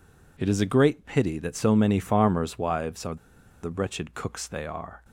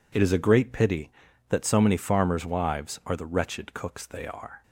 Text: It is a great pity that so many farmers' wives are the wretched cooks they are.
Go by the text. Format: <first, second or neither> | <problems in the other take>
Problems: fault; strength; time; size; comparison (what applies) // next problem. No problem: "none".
second | pauses between "are" and "the"; noticeable; at 3.1 s; 0.47 s long